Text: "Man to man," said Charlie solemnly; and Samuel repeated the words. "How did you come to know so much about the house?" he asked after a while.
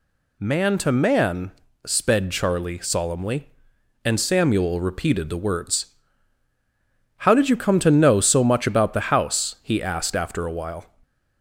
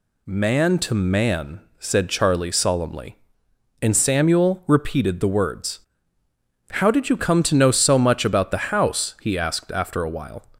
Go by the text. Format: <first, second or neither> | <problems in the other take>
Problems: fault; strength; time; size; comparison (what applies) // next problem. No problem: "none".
second | says "sped" for "said"; at 1.8 s